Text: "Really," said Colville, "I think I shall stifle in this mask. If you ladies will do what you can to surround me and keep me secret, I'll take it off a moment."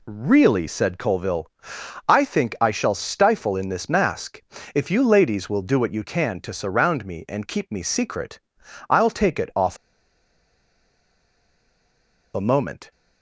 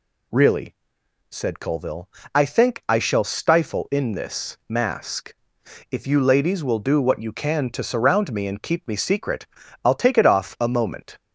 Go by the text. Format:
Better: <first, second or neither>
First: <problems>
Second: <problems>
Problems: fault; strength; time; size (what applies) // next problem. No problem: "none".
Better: second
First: pauses between "off" and "a"; strong; at 9.7 s; 2.5 s long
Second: none